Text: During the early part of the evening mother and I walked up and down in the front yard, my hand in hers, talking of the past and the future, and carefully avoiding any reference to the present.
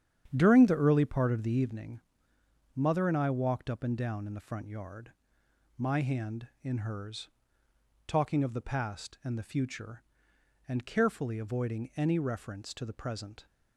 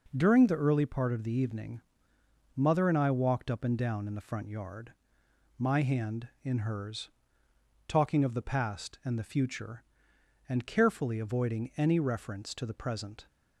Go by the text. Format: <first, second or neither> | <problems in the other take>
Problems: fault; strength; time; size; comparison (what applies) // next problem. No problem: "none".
second | starts louder than the rest; strong; until 1.7 s; 9 dB // pauses between "evening" and "mother"; noticeable; at 2.0 s; 0.74 s long; noticeable in the second